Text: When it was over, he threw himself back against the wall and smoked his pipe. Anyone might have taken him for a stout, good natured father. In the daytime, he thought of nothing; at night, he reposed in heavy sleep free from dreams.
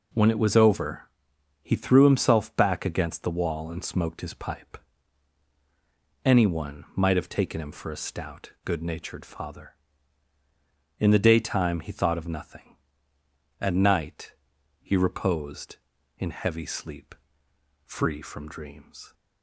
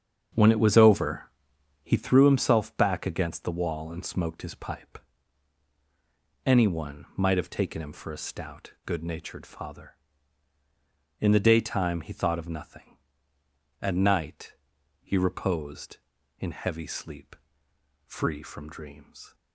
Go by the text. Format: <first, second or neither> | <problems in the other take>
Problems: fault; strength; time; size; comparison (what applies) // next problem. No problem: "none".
first | starts louder than the rest; strong; until 2.1 s; 7 dB // pauses between "sleep" and "free"; noticeable; at 17.3 s; 0.70 s long; noticeable in the first